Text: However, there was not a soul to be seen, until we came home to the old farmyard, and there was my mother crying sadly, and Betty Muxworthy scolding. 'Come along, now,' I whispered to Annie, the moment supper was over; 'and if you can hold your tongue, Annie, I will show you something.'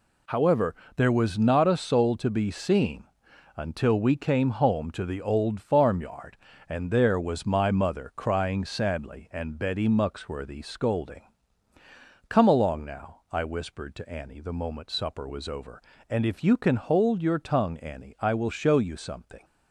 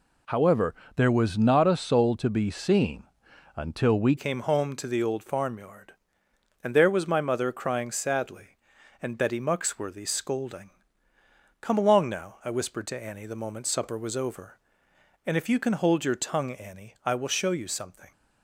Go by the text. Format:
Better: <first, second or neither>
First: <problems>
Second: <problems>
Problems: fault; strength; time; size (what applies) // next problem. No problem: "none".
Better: first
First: none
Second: changes voice at "came"; from 4.1 s on; 14.0 s long